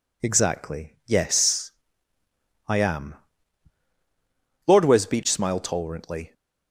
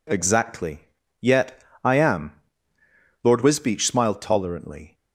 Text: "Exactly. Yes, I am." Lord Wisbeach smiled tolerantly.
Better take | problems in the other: first | says "Yet" for "Yes"; at 1.2 s

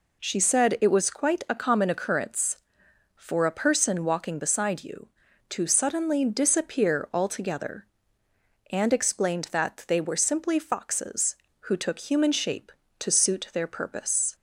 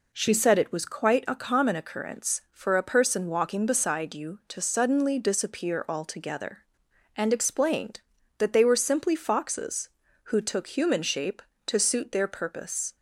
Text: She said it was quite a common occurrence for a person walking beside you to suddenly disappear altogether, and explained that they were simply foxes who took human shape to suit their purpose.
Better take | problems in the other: neither | none

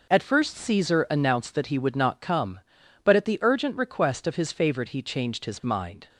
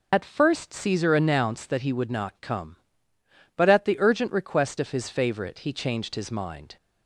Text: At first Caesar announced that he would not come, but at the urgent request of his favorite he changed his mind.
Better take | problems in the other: first | loses the start of "At"; at 0.1 s; 40 ms

